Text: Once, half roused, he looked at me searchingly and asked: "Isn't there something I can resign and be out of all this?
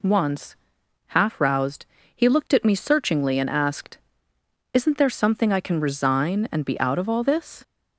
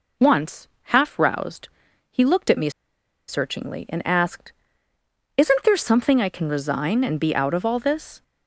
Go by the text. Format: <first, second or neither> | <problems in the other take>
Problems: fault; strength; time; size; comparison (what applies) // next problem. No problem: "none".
first | pauses between "me" and "searchingly"; noticeable; at 2.7 s; 0.57 s long